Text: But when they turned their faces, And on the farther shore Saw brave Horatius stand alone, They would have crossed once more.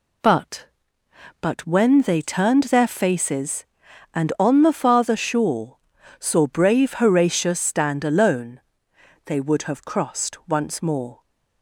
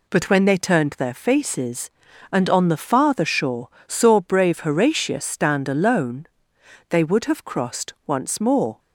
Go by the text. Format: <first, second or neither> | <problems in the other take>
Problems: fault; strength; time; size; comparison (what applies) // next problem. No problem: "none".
second | says "But" twice; at 1.4 s // pauses between "shore" and "Saw"; at 5.7 s; 0.42 s long; slight in the second